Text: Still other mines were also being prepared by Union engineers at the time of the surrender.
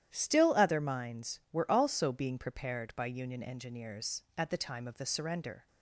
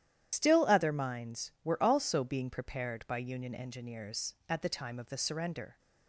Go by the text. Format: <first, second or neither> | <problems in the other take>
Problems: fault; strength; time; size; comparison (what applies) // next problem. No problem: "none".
first | loses the start of "Still"; at 0.3 s; 85 ms // starts louder than the rest; strong; until 1.3 s; 11 dB; strong in the first